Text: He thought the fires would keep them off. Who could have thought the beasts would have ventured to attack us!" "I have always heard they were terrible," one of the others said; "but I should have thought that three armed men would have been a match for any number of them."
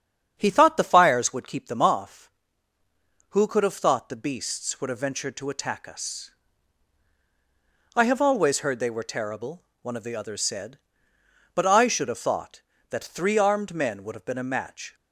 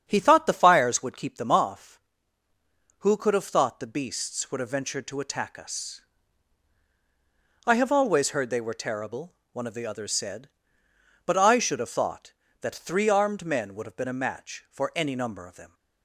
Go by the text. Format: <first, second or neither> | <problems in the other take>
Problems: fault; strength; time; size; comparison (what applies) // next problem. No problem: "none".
second | starts louder than the rest; strong; until 1.3 s; 8 dB; strong in the second // stops before "for any number of them"; at 14.9 s